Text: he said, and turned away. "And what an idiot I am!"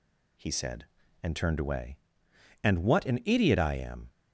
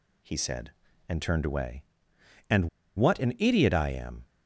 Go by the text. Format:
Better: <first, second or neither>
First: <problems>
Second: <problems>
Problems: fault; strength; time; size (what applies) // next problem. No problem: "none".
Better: first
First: none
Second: pauses between "And" and "what"; slight; at 2.6 s; 0.28 s long